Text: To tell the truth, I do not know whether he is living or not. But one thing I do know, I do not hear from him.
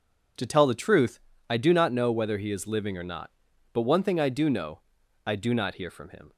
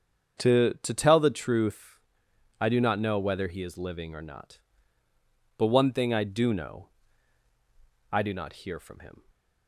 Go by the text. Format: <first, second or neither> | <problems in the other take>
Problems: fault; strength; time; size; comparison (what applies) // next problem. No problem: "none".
first | starts louder than the rest; strong; until 1.4 s; 7 dB // says "To" twice; at 0.8 s